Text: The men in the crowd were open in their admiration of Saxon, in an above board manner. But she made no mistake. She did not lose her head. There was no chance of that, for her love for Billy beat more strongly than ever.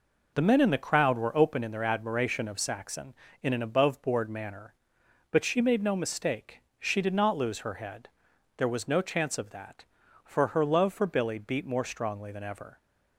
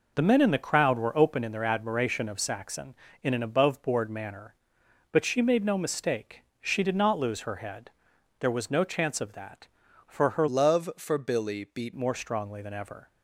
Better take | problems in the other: first | changes voice from "love" to "beat"; from 10.4 to 11.9 s; 1.5 s long

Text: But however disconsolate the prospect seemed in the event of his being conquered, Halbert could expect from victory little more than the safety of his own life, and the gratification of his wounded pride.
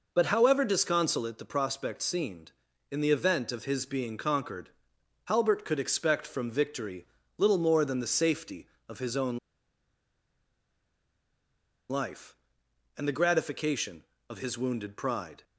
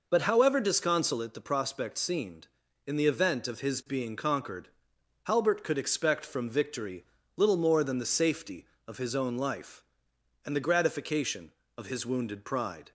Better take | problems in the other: second | pauses between "victory" and "little"; slight; at 7.0 s; 0.32 s long; slight in the second // pauses between "own" and "life"; strong; at 9.3 s; 2.5 s long

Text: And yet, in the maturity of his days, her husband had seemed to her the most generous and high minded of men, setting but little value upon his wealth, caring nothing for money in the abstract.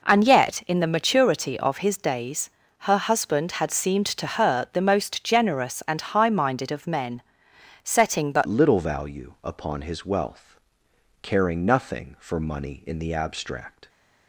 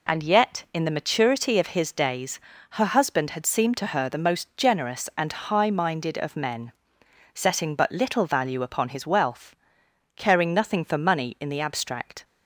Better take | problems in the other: second | changes voice at "little"; from 8.4 s on; 5.4 s long

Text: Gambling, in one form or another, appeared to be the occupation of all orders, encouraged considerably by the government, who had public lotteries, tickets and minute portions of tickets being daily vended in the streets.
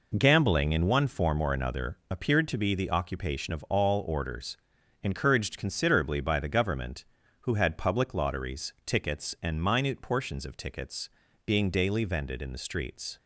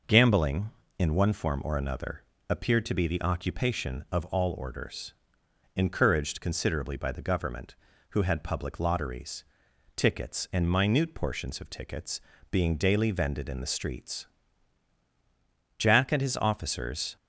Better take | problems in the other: first | pauses between "tickets" and "being"; slight; at 12.1 s; 0.32 s long; also in the first // goes on to say "Jack and his officers"; from 15.7 s on; 1.3 s long

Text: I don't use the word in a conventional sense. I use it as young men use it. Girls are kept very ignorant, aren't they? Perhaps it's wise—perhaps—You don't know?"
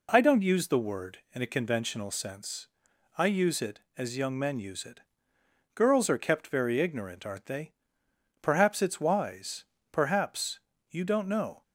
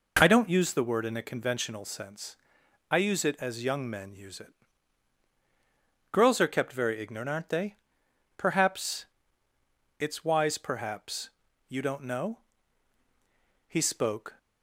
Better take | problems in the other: first | pauses between "Perhaps" and "it's"; noticeable; at 9.0 s; 0.94 s long // goes on to say "He spoke"; noticeable; from 13.6 s on; 0.70 s long

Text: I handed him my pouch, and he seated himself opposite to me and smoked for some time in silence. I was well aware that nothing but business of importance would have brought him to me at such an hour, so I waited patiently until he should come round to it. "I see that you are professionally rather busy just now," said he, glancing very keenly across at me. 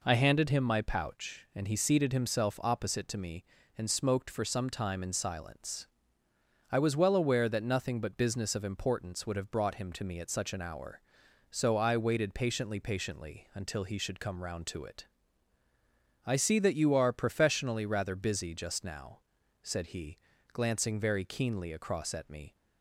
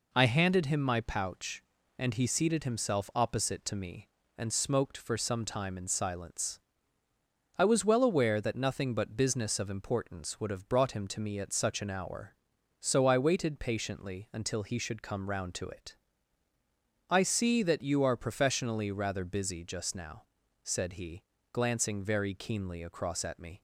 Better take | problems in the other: second | says "patiently" twice; at 12.8 s

